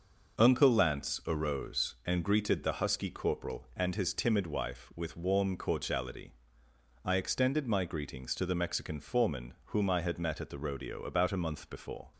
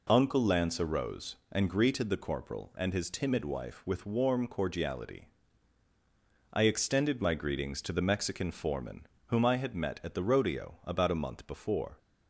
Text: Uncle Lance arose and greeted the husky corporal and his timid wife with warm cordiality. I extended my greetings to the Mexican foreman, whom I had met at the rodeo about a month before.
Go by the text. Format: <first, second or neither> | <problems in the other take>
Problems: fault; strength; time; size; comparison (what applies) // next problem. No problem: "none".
first | skips "husky"; at 2.1 s